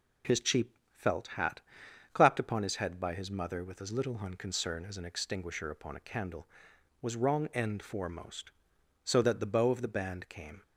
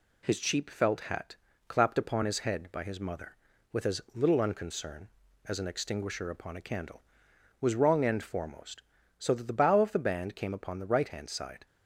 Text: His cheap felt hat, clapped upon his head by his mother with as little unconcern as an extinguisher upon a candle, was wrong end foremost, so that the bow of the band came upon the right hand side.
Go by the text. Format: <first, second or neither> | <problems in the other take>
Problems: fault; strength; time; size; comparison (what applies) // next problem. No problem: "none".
second | pauses between "cheap" and "felt"; slight; at 0.7 s; 0.16 s long // stops before "upon the right hand side"; at 10.6 s